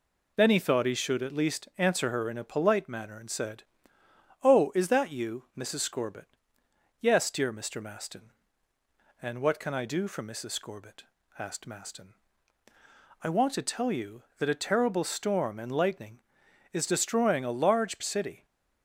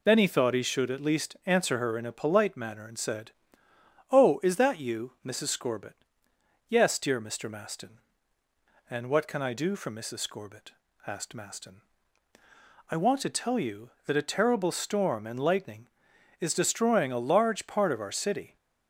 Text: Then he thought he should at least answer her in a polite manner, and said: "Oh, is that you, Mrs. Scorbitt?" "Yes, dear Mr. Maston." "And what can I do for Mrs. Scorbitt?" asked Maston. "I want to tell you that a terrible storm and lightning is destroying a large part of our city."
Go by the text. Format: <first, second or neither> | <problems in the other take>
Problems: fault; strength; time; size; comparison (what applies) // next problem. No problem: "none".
second | skips "part of our"; at 17.9 s